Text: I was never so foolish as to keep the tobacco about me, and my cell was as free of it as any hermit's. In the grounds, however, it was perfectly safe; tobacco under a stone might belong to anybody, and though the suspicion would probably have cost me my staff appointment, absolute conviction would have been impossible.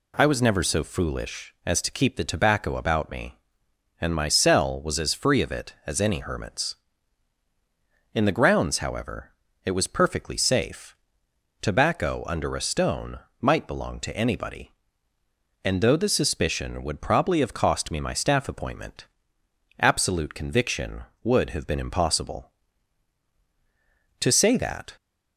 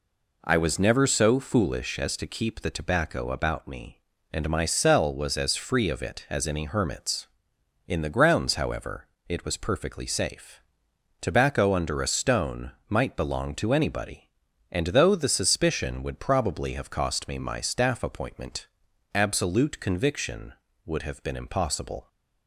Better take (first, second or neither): second